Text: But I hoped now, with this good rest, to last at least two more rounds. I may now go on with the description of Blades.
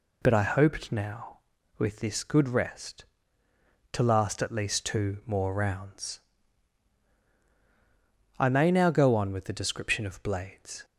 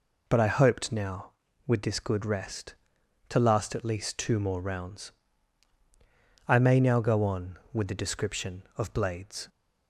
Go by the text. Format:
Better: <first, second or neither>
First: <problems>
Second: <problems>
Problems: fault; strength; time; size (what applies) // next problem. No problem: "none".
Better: neither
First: none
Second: none